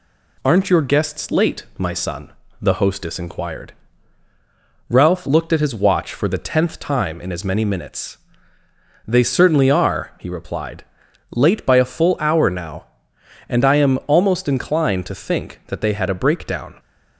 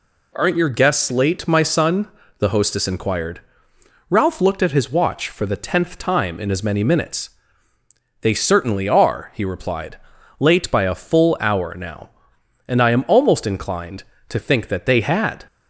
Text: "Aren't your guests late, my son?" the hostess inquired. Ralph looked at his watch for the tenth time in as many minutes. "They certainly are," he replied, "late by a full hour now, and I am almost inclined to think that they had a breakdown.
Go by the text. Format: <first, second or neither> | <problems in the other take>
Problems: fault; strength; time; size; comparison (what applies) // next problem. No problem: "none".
first | stops before "a breakdown"; at 15.4 s